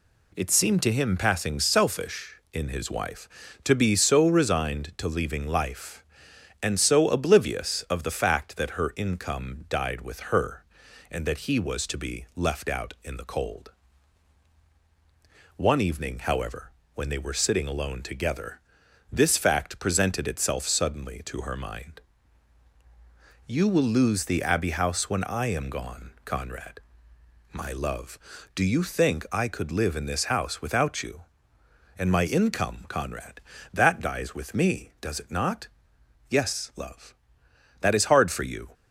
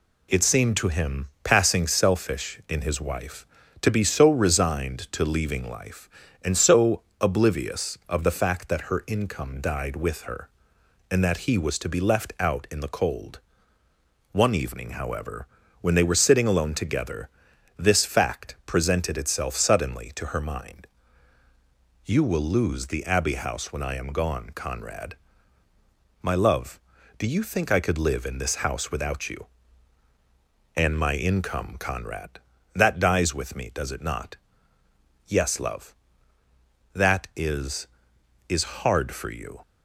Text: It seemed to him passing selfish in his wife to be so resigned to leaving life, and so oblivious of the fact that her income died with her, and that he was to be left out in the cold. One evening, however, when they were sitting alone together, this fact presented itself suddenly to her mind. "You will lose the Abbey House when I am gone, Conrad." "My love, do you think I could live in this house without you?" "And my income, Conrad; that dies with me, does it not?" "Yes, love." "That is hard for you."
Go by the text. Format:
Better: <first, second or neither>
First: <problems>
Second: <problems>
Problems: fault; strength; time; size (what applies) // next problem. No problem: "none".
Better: first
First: none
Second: pauses between "so" and "oblivious"; slight; at 7.0 s; 0.18 s long // says "is" twice; at 38.4 s